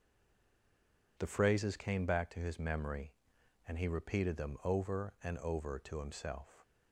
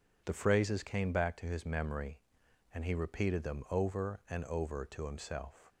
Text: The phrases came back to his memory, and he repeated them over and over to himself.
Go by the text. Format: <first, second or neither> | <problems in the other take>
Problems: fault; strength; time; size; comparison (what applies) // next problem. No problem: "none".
second | stays silent before the first word; noticeable; until 1.1 s; 1.1 s long